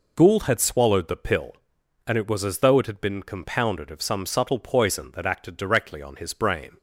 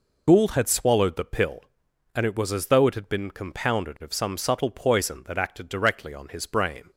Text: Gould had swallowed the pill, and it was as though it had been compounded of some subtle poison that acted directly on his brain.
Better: first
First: none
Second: loses the start of "Gould"; at 0.2 s; 25 ms

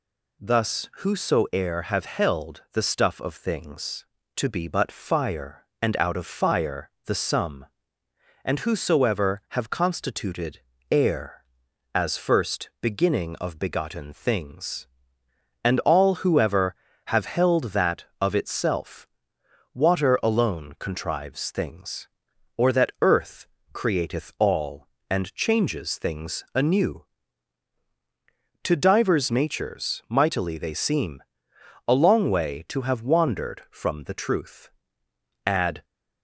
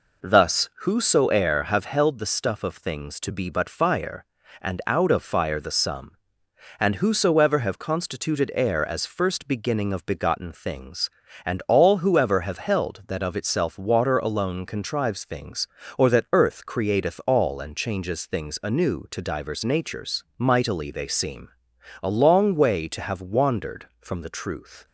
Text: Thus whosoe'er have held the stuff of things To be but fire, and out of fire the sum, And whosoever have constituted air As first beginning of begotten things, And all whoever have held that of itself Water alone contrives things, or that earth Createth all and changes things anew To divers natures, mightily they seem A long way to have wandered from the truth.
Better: second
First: pauses between "fire" and "the"; slight; at 6.8 s; 0.16 s long // pauses between "constituted" and "air"; slight; at 10.5 s; 0.32 s long // pauses between "itself" and "Water"; noticeable; at 19.0 s; 0.66 s long // pauses between "earth" and "Createth"; slight; at 23.4 s; 0.24 s long // pauses between "seem" and "A"; noticeable; at 31.2 s; 0.64 s long // goes on to say "Add"; slight; from 35.4 s on; 0.38 s long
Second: pauses between "seem" and "A"; noticeable; at 21.4 s; 0.54 s long

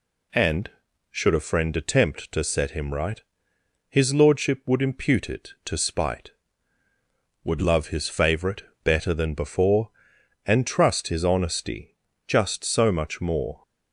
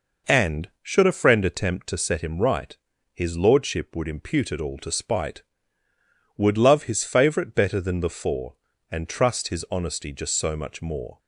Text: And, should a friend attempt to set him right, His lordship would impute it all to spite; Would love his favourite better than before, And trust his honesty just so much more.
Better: second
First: skips "all"; at 5.5 s // pauses between "favourite" and "better"; slight; at 8.6 s; 0.22 s long // pauses between "honesty" and "just"; slight; at 11.9 s; 0.32 s long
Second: none

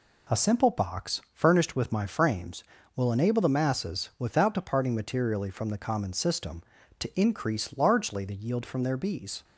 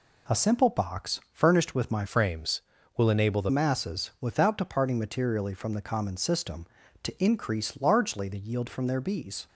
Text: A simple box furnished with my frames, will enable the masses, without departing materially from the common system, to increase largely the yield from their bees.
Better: first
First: none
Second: changes voice from "frames" to "the"; from 2.0 to 3.4 s; 1.4 s long

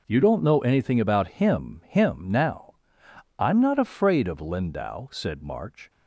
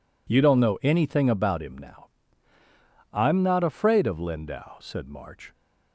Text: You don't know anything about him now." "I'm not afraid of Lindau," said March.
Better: second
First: says "him" twice; at 1.8 s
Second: none

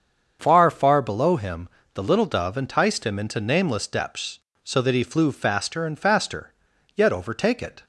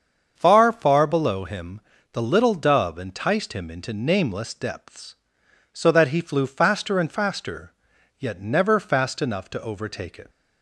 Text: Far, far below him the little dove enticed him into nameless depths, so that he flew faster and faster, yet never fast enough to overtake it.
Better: second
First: starts louder than the rest; until 1.4 s; 7 dB // pauses between "him" and "the"; slight; at 1.6 s; 0.26 s long // skips "never fast enough to"; at 7.1 s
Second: starts louder than the rest; until 1.3 s; 7 dB // pauses between "him" and "the"; slight; at 1.8 s; 0.30 s long

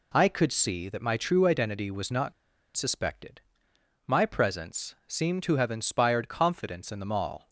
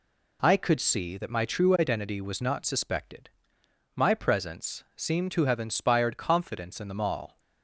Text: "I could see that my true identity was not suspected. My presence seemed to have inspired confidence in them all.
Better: second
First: pauses between "not" and "suspected"; at 2.3 s; 0.43 s long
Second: none

